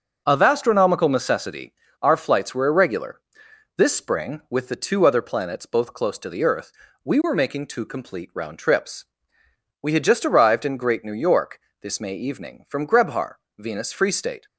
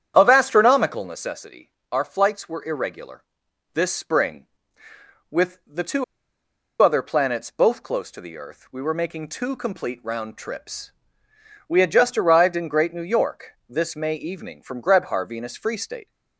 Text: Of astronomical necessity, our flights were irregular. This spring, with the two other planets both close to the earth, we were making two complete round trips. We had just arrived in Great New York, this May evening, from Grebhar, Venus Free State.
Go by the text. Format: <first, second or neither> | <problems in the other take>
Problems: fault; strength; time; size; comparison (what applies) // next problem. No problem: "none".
first | starts louder than the rest; strong; until 1.1 s; 9.5 dB // pauses between "two" and "other"; noticeable; at 6.0 s; 0.78 s long